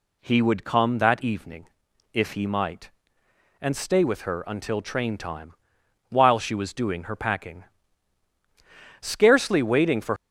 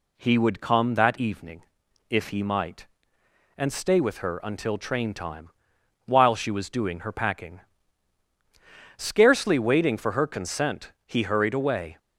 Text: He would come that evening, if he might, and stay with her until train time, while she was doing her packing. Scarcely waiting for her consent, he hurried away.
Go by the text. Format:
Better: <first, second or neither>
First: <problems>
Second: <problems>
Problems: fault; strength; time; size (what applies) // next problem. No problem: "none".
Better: second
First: stops before "her consent he hurried away"; at 10.1 s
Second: none